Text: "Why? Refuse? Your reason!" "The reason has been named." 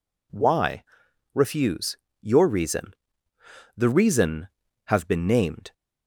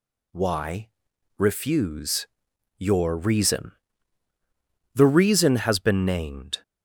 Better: second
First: says "have" for "has"; at 4.8 s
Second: none

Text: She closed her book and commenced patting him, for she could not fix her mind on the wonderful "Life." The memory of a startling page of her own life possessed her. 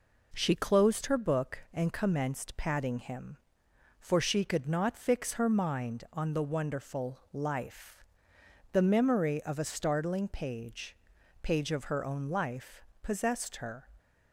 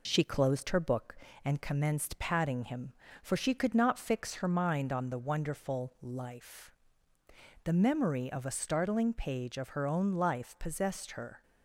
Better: second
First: pauses between "wonderful" and "Life"; slight; at 7.1 s; 0.16 s long // says "page" twice; at 11.4 s // pauses between "life" and "possessed"; slight; at 12.8 s; 0.20 s long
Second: none

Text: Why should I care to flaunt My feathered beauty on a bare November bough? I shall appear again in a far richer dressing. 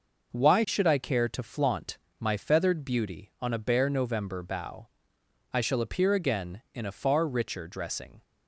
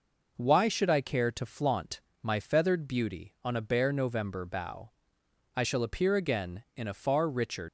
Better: first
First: pauses between "flaunt" and "My"; slight; at 1.9 s; 0.20 s long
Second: pauses between "flaunt" and "My"; slight; at 2.0 s; 0.20 s long // stops before "dressing"; at 7.6 s

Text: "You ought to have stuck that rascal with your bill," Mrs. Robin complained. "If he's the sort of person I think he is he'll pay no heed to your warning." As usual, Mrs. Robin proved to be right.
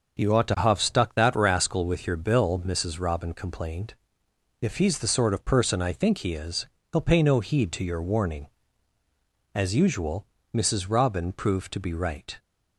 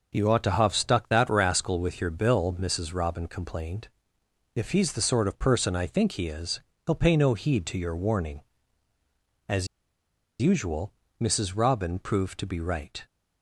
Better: first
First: pauses between "is" and "he'll"; slight; at 6.6 s; 0.26 s long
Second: pauses between "is" and "he'll"; slight; at 6.5 s; 0.26 s long // pauses between "As" and "usual"; noticeable; at 9.6 s; 0.73 s long

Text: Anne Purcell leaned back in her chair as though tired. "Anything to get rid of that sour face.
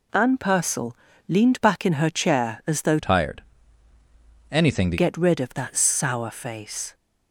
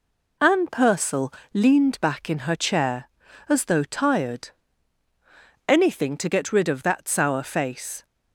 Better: second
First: pauses between "Purcell" and "leaned"; slight; at 0.9 s; 0.32 s long // changes voice from "tired" to "to"; from 3.0 to 4.9 s; 1.9 s long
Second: pauses between "Purcell" and "leaned"; slight; at 1.3 s; 0.20 s long

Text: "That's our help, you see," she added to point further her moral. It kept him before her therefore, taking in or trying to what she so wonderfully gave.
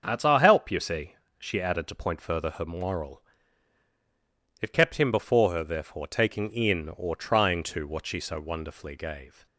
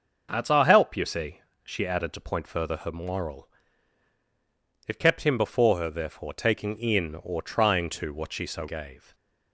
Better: first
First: starts louder than the rest; until 1.0 s; 6.5 dB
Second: starts louder than the rest; noticeable; until 1.3 s; 6 dB // skips "wonderfully"; at 8.6 s // stays silent after the last word; slight; from 8.9 s on; 0.6 s long

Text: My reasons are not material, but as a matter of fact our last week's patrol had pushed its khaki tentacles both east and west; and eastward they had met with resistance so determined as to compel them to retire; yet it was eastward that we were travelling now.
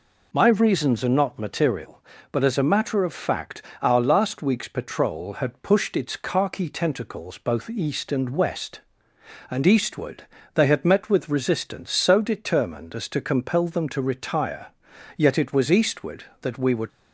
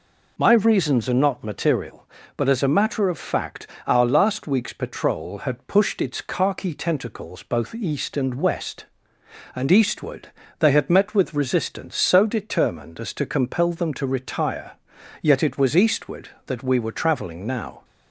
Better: second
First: pauses between "fact" and "our"; slight; at 3.6 s; 0.20 s long // pauses between "eastward" and "they"; slight; at 10.2 s; 0.30 s long // stops before "travelling now"; at 16.8 s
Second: pauses between "fact" and "our"; slight; at 3.6 s; 0.20 s long // pauses between "eastward" and "they"; slight; at 10.2 s; 0.30 s long

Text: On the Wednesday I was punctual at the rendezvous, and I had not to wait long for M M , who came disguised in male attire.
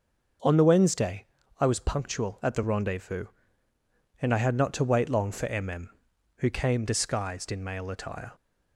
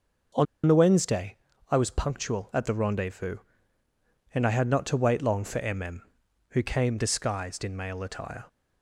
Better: first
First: starts louder than the rest; until 1.7 s; 6 dB // pauses between "Wednesday" and "I"; slight; at 1.2 s; 0.34 s long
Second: starts louder than the rest; noticeable; until 1.9 s; 6 dB // pauses between "On" and "the"; slight; at 0.4 s; 0.21 s long // pauses between "Wednesday" and "I"; slight; at 1.3 s; 0.34 s long

